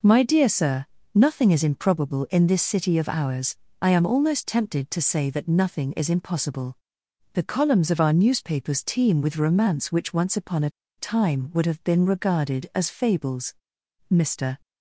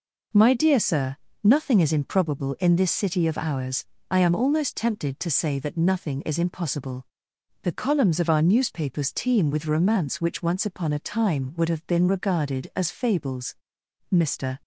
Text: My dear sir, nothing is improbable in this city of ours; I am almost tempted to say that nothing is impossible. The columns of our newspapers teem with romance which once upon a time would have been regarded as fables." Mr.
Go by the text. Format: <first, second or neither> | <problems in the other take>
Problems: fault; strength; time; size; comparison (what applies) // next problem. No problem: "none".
second | pauses between "a" and "time"; slight; at 10.7 s; 0.27 s long